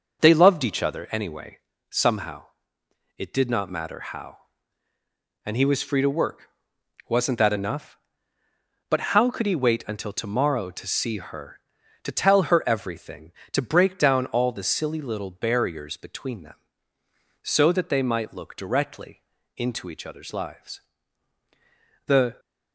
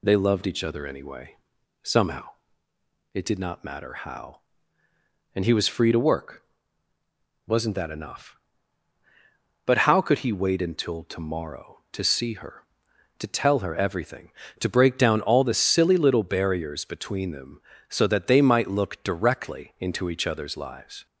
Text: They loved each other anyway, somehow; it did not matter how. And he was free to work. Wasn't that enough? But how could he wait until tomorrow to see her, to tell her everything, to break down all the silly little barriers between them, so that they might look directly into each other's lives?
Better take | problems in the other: second | pauses between "But" and "how"; slight; at 8.9 s; 0.16 s long // pauses between "directly" and "into"; slight; at 19.2 s; 0.34 s long // goes on to say "The"; slight; from 22.0 s on; 0.32 s long

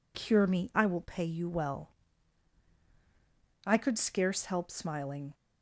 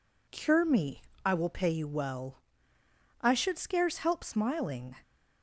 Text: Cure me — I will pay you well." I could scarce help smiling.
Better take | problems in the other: first | says "should" for "could"; at 3.3 s

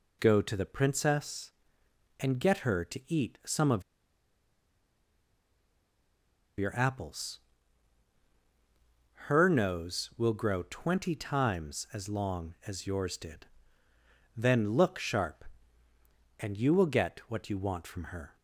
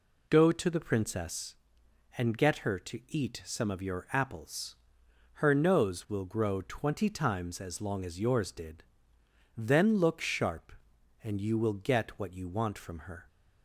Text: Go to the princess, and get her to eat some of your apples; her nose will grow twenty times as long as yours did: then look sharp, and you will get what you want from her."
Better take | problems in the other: second | pauses between "of" and "your"; strong; at 3.8 s; 2.7 s long

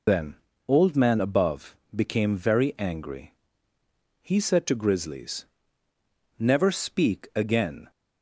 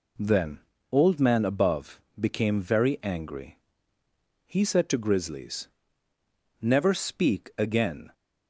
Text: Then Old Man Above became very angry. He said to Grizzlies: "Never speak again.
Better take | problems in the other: second | loses the start of "Then"; at 0.0 s; 155 ms // pauses between "Then" and "Old"; slight; at 0.3 s; 0.30 s long; slight in the second // pauses between "Above" and "became"; slight; at 1.7 s; 0.18 s long; slight in the second

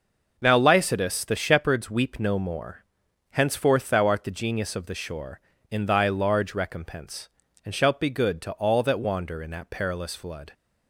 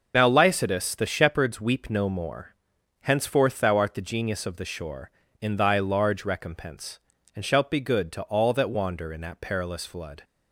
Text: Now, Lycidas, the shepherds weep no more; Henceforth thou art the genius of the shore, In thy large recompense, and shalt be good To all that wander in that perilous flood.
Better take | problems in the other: first | loses the start of "Now"; at 0.1 s; 50 ms

